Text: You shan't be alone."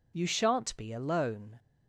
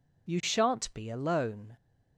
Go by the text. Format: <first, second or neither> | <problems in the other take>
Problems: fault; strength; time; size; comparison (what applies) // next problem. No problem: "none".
neither | none